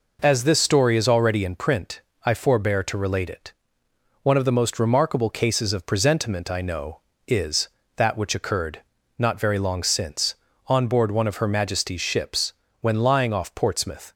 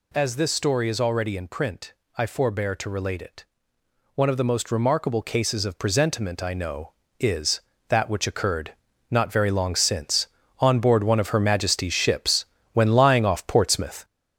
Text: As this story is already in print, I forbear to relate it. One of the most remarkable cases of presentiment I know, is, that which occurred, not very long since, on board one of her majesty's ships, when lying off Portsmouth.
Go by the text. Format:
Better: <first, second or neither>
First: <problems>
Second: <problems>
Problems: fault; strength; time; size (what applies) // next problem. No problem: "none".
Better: first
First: none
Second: gets louder; noticeable; throughout; 6 dB